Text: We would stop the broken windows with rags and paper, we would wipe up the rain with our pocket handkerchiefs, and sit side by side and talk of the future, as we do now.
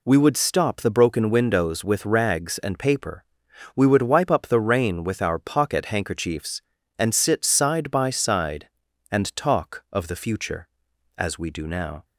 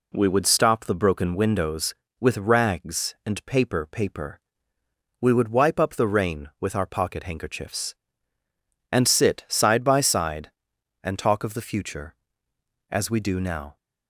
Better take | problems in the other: first | says "paper" twice; at 3.9 s

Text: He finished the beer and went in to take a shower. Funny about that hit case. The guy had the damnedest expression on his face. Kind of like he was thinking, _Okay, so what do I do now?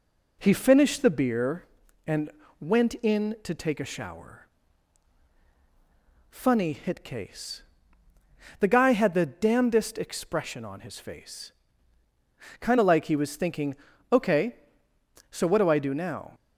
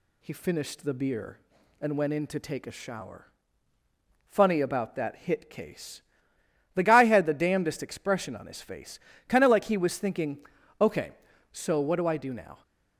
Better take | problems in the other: second | pauses between "and" and "went"; slight; at 2.2 s; 0.30 s long // skips "about that"; at 6.7 s

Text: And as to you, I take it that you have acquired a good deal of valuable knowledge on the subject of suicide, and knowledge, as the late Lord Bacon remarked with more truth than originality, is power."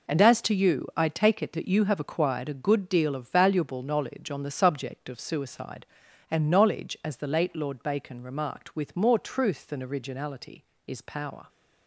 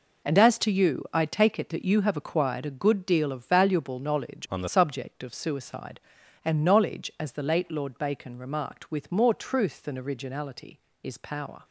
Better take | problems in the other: first | changes voice from "on" to "the"; from 4.5 to 4.6 s; 0.1 s long

